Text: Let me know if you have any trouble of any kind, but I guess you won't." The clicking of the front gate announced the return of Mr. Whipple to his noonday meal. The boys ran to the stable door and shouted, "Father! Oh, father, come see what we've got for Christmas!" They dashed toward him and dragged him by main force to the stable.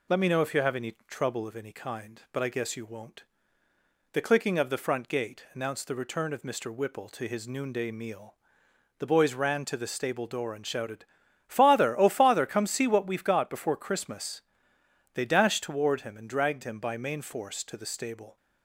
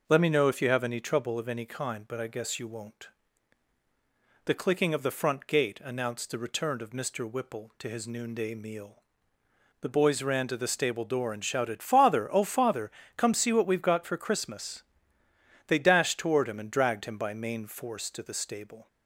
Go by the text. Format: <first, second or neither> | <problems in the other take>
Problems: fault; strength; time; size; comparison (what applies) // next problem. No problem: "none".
second | says "before" for "for"; at 13.4 s